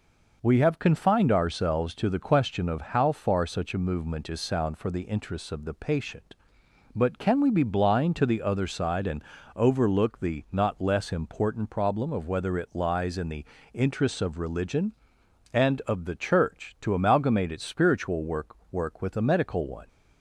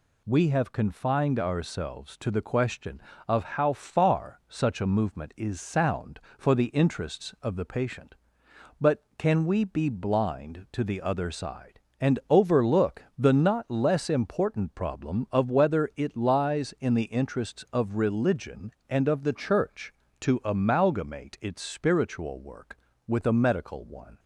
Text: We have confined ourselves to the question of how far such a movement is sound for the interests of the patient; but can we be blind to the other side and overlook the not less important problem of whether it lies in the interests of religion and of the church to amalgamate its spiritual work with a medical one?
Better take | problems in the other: second | pauses between "and" and "overlook"; slight; at 9.2 s; 0.32 s long // pauses between "the" and "interests"; slight; at 13.4 s; 0.28 s long // says "work" twice; at 18.7 s

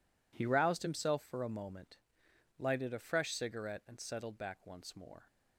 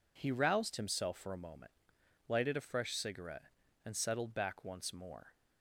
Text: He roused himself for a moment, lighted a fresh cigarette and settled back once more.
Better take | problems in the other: neither | none

